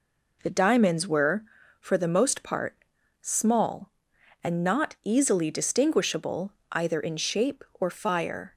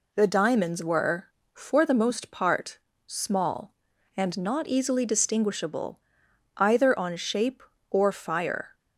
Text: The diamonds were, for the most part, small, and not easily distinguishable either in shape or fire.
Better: first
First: pauses between "distinguishable" and "either"; slight; at 6.5 s; 0.20 s long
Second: pauses between "distinguishable" and "either"; noticeable; at 5.9 s; 0.60 s long // says "on" for "in"; at 6.9 s

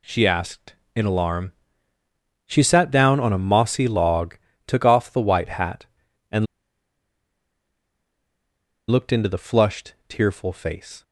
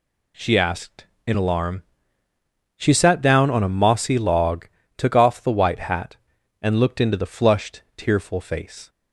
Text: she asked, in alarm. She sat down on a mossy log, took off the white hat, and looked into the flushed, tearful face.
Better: second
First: pauses between "and" and "looked"; strong; at 6.4 s; 2.4 s long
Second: none

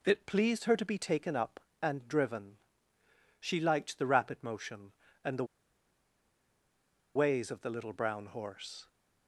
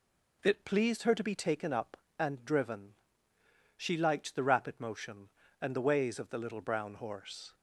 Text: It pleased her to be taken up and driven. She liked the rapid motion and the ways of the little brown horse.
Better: second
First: pauses between "the" and "ways"; strong; at 5.4 s; 1.7 s long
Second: none

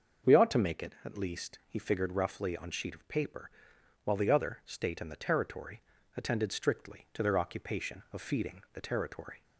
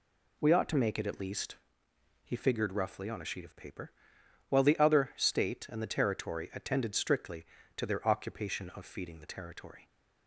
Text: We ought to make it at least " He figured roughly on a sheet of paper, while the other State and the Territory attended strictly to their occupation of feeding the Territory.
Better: second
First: starts louder than the rest; until 1.3 s; 6 dB // skips "a"; at 2.7 s // pauses between "Territory" and "attended"; slight; at 5.8 s; 0.34 s long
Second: none

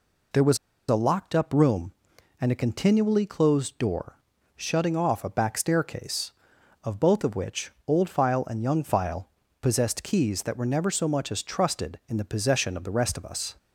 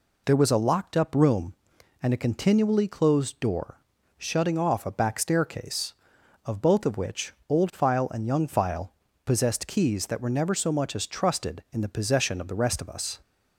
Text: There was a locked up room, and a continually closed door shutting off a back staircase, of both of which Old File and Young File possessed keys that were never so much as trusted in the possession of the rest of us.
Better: second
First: pauses between "was" and "a"; slight; at 0.5 s; 0.31 s long // pauses between "door" and "shutting"; slight; at 4.1 s; 0.36 s long // pauses between "which" and "Old"; slight; at 7.7 s; 0.16 s long // pauses between "File" and "possessed"; slight; at 9.2 s; 0.32 s long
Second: pauses between "door" and "shutting"; slight; at 3.7 s; 0.36 s long // pauses between "which" and "Old"; slight; at 7.3 s; 0.16 s long // pauses between "File" and "possessed"; slight; at 8.9 s; 0.32 s long

